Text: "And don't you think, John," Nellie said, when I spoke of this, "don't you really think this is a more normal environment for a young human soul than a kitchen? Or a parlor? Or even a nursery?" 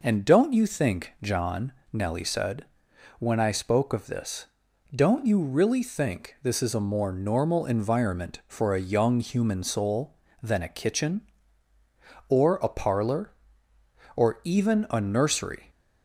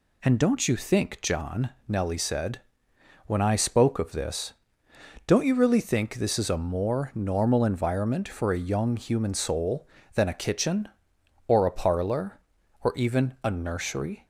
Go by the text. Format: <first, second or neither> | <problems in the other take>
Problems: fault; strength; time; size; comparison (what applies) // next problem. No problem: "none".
neither | none